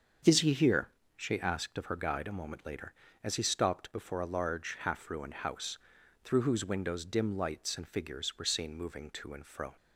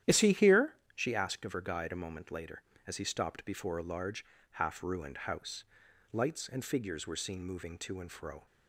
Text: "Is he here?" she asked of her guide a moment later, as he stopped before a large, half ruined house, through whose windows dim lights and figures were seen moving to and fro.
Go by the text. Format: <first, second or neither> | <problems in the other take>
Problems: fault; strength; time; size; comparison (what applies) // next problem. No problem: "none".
first | starts louder than the rest; strong; until 1.2 s; 11 dB; also in the first // skips "through whose windows dim"; at 5.8 s